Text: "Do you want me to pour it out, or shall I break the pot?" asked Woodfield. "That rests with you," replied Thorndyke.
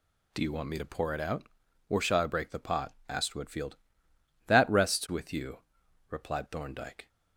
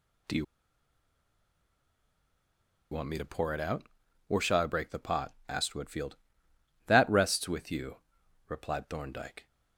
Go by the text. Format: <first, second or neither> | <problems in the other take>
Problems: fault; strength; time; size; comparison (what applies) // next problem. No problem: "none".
first | pauses between "you" and "want"; strong; at 0.4 s; 2.4 s long